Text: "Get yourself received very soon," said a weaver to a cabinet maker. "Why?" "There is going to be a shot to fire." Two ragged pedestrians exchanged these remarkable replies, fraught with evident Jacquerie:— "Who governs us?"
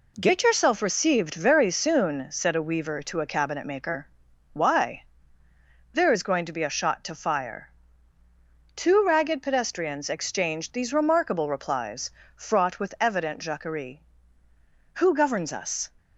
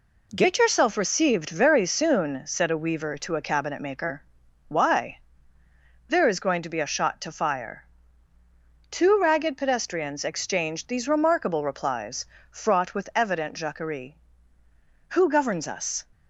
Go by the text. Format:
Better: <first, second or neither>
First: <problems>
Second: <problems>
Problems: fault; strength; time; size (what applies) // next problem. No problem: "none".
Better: neither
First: none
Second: none